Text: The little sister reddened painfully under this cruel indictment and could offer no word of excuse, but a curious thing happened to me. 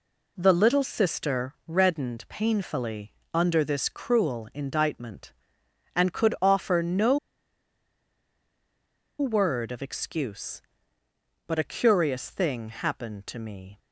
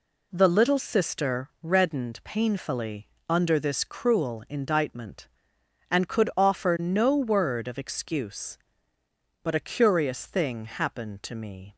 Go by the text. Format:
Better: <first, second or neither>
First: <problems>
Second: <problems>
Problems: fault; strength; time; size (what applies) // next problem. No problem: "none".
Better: second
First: pauses between "painfully" and "under"; slight; at 3.1 s; 0.20 s long // pauses between "no" and "word"; strong; at 7.1 s; 2.0 s long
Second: pauses between "painfully" and "under"; slight; at 3.0 s; 0.20 s long